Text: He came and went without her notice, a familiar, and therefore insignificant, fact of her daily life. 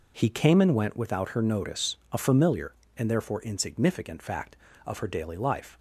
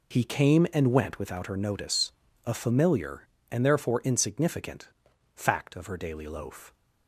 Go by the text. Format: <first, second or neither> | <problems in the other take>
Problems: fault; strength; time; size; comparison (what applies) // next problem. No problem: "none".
first | says "loaf" for "life"; at 6.2 s